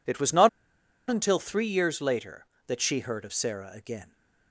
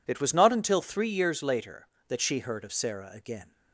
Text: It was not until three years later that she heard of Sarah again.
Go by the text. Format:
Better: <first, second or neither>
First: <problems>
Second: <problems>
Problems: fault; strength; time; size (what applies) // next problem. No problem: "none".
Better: second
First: pauses between "not" and "until"; noticeable; at 0.4 s; 0.59 s long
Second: none